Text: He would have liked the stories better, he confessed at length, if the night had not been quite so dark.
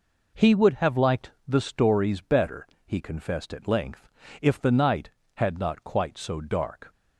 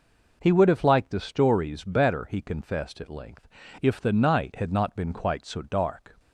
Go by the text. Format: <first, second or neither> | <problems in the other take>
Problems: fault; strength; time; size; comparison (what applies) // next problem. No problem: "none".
second | pauses between "liked" and "the"; slight; at 1.2 s; 0.18 s long // skips "been"; at 5.8 s